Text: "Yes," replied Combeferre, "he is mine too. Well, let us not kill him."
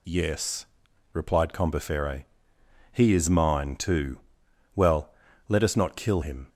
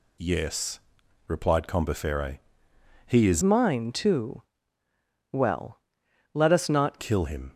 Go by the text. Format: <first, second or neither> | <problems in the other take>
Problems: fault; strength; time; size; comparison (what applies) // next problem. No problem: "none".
first | changes voice from "mine" to "not"; from 3.4 to 6.9 s; 3.5 s long